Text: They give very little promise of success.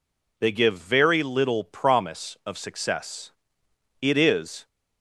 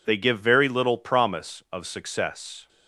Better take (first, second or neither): second